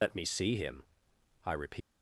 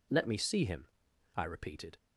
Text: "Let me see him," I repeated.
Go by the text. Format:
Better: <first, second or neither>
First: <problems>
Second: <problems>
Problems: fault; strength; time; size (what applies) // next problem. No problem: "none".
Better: second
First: loses the start of "Let"; at 0.0 s; 80 ms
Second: none